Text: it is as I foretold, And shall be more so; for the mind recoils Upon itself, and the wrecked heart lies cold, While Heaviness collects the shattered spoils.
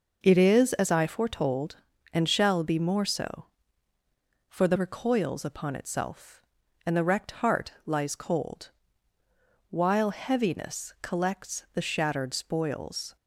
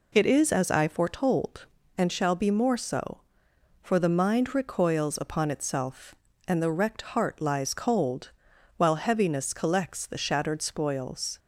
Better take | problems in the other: second | skips "mind"; at 4.7 s

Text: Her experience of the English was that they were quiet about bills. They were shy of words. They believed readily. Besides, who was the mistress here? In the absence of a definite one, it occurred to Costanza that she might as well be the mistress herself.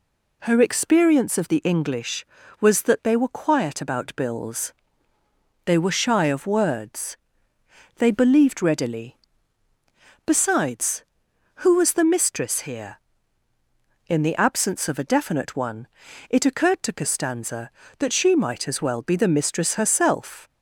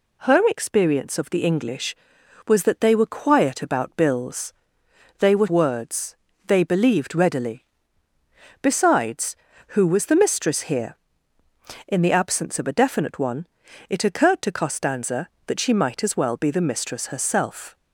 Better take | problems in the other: first | skips "shy of"; at 5.4 s

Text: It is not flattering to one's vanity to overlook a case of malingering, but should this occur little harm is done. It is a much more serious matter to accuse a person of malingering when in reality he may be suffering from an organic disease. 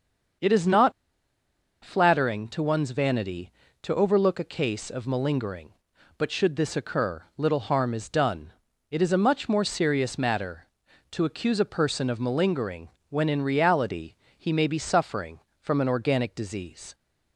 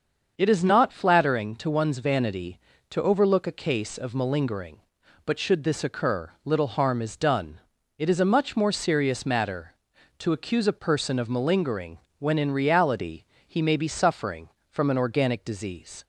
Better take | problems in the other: second | starts louder than the rest; until 2.3 s; 7 dB; also in the second // pauses between "not" and "flattering"; noticeable; at 0.9 s; 0.91 s long // pauses between "malingering" and "when"; slight; at 12.8 s; 0.22 s long; slight in the second // pauses between "reality" and "he"; slight; at 14.1 s; 0.24 s long; slight in the second

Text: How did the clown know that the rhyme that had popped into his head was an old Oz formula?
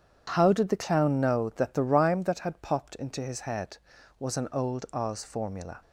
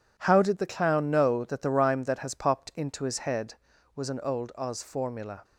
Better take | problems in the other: first | says "has" for "had"; at 2.1 s

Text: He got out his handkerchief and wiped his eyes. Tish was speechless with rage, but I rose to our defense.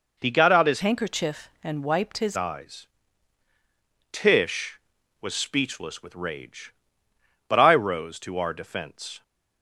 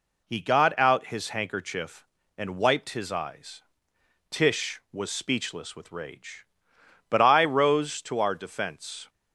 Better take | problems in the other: second | changes voice from "handkerchief" to "his"; from 0.8 to 2.3 s; 1.5 s long

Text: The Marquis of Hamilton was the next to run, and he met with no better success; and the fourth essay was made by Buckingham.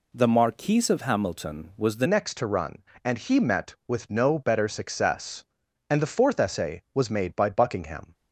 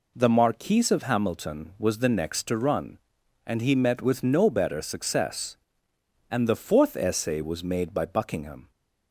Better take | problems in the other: second | changes voice at "next"; from 2.0 s on; 6.1 s long

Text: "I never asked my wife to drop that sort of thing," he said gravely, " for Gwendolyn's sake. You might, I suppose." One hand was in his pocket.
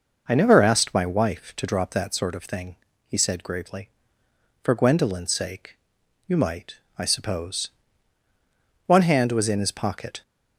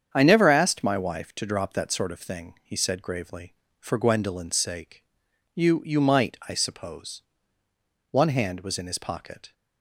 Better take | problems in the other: first | starts louder than the rest; strong; until 1.1 s; 8 dB; noticeable in the first // says "You" twice; at 5.8 s

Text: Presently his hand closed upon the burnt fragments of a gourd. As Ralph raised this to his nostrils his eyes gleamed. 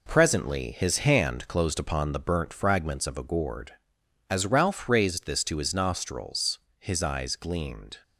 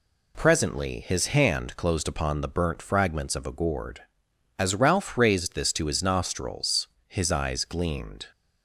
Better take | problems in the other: second | gets quieter; noticeable; throughout; 5.5 dB // pauses between "nostrils" and "his"; slight; at 6.5 s; 0.20 s long; slight in the second

